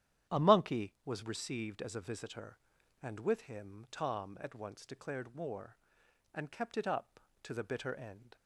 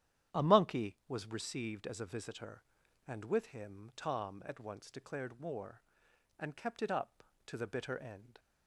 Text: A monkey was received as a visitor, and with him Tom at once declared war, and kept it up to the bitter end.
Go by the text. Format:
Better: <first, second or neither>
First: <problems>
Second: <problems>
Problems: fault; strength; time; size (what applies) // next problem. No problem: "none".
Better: neither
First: starts louder than the rest; strong; until 1.4 s; 10.5 dB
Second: starts louder than the rest; strong; until 1.4 s; 10.5 dB